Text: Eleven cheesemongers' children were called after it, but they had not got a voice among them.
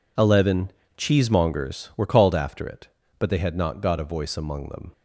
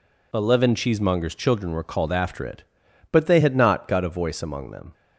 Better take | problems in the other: second | pauses between "Eleven" and "cheesemongers"; slight; at 0.7 s; 0.24 s long // skips "children"; at 1.9 s

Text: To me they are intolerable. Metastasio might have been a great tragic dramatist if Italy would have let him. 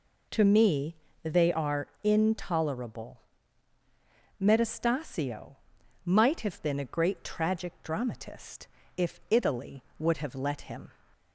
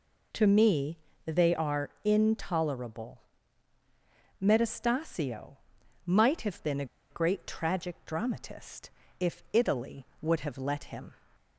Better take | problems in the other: first | pauses between "me" and "they"; slight; at 0.9 s; 0.28 s long; slight in the first // pauses between "are" and "intolerable"; slight; at 1.8 s; 0.16 s long; slight in the first // pauses between "Metastasio" and "might"; noticeable; at 5.5 s; 0.48 s long; noticeable in the first // pauses between "a" and "great"; slight; at 6.8 s; 0.25 s long // pauses between "dramatist" and "if"; slight; at 8.8 s; 0.30 s long; slight in the first

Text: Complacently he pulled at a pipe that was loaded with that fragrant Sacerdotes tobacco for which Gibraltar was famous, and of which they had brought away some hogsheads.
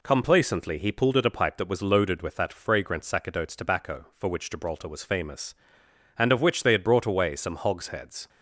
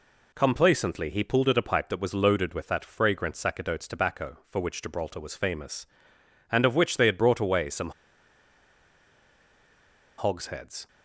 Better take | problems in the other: first | pauses between "some" and "hogsheads"; strong; at 7.9 s; 2.2 s long

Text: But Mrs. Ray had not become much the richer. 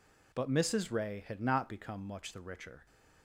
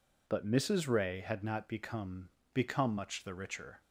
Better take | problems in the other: first | says "become" twice; at 2.5 s

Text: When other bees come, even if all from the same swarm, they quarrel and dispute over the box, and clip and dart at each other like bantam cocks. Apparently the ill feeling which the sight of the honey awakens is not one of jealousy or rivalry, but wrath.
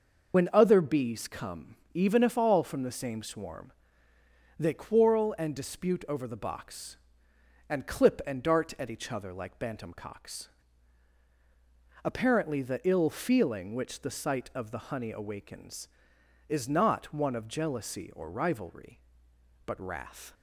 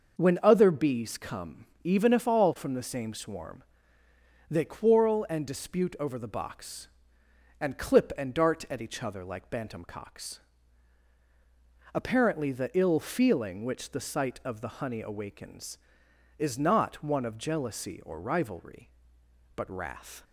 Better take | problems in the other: second | loses the start of "When"; at 0.3 s; 65 ms // starts louder than the rest; noticeable; until 1.3 s; 6 dB; noticeable in the second

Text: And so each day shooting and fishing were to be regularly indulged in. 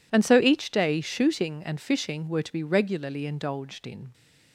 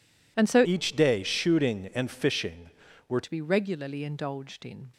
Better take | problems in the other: first | changes voice from "each" to "were"; from 0.6 to 3.1 s; 2.5 s long

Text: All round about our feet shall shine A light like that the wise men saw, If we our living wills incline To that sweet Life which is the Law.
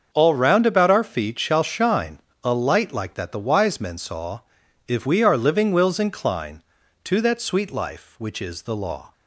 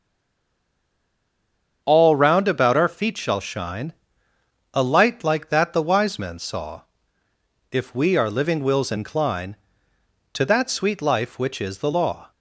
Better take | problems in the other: first | stays silent before the first word; noticeable; until 1.8 s; 1.8 s long // starts louder than the rest; strong; until 2.8 s; 7.5 dB; also in the first // pauses between "shine" and "A"; noticeable; at 3.9 s; 0.80 s long; slight in the first

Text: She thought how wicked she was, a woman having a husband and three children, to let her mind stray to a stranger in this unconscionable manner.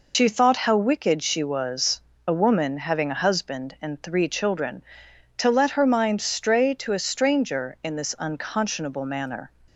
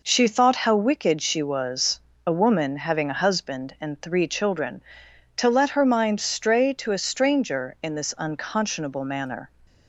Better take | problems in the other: second | loses the start of "She"; at 0.1 s; 95 ms

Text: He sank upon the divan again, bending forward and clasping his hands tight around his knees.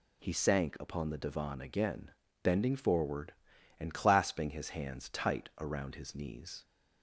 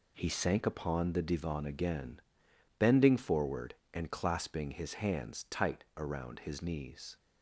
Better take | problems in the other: neither | none

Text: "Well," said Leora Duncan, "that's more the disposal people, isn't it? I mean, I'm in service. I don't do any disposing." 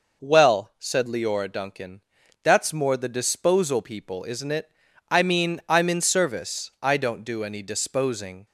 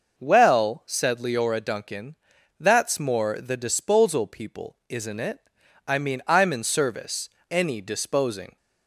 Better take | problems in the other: first | skips "I don't do"; at 7.3 s

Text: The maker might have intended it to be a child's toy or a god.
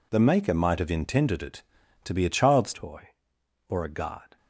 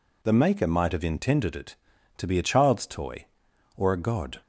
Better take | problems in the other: second | changes voice at "toy"; from 2.7 s on; 1.6 s long

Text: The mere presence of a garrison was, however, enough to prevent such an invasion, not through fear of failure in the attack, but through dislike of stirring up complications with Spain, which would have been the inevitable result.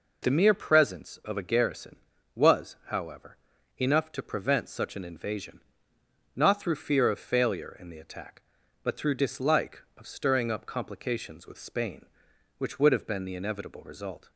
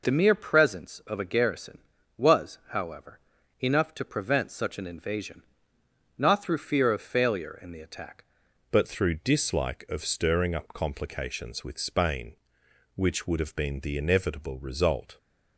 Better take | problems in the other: first | changes voice at "but"; from 8.6 s on; 6.5 s long

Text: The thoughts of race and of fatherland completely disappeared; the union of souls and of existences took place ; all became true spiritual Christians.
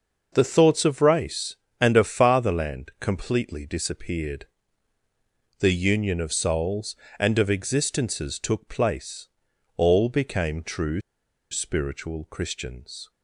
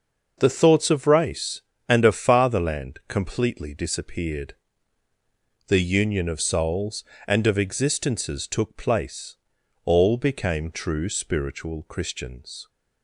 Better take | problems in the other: second | pauses between "true" and "spiritual"; noticeable; at 11.0 s; 0.51 s long

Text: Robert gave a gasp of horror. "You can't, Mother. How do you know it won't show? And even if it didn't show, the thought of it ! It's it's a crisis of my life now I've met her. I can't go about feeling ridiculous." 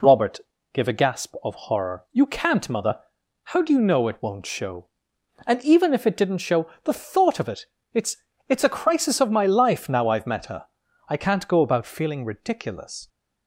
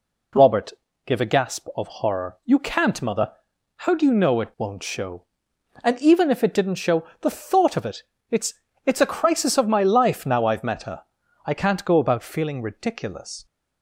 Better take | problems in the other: neither | pauses between "Robert" and "gave"; slight; the same in both // pauses between "It's" and "it's"; slight; the same in both

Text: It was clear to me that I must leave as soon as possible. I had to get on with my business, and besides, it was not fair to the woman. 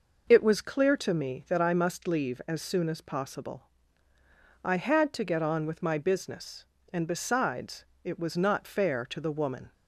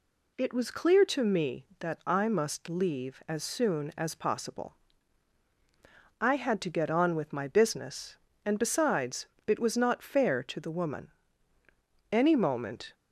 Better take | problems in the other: first | goes on to say "Any moment"; noticeable; from 12.1 s on; 0.82 s long

